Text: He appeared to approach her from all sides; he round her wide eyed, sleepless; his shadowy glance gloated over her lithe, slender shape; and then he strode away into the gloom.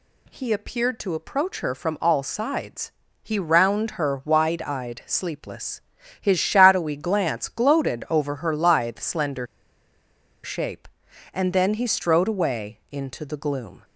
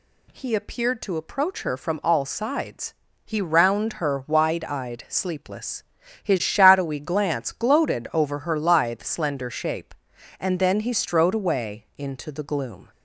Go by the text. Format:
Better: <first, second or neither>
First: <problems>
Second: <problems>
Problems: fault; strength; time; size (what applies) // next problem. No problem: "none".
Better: second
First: pauses between "slender" and "shape"; noticeable; at 9.4 s; 0.97 s long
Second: none